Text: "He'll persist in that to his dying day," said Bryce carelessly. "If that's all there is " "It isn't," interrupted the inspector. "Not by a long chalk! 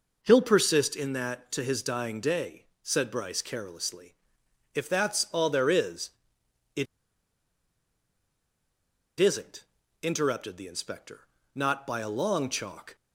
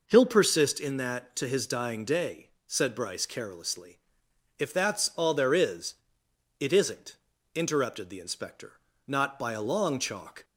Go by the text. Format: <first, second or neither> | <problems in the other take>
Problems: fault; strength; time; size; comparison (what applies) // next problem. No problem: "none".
second | pauses between "It" and "isn't"; strong; at 6.8 s; 2.3 s long